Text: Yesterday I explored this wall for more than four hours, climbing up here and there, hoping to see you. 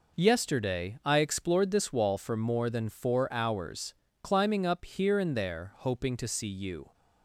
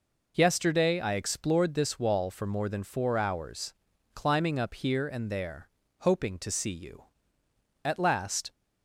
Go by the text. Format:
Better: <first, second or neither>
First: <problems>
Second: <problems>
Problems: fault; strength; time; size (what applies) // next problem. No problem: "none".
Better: first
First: none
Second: goes on to say "At last"; noticeable; from 7.8 s on; 0.66 s long